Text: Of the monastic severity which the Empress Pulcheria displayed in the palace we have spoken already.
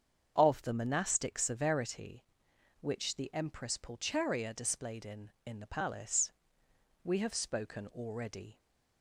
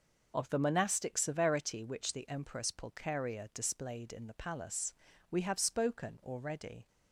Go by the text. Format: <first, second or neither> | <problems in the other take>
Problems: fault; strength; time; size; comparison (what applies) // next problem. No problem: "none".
second | starts louder than the rest; strong; until 1.3 s; 7 dB // says "in" twice; at 5.4 s // pauses between "palace" and "we"; noticeable; at 6.3 s; 0.72 s long; also in the second